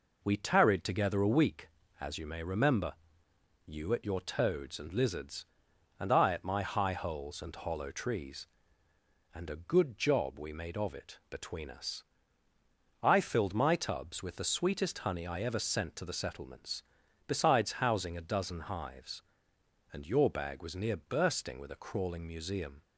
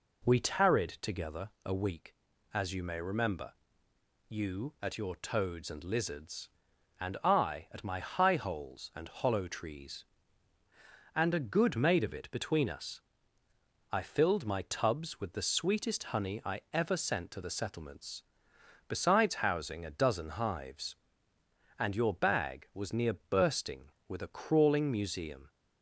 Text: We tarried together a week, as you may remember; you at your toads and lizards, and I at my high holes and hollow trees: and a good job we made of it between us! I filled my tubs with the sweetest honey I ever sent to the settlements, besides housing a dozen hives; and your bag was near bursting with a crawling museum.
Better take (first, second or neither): first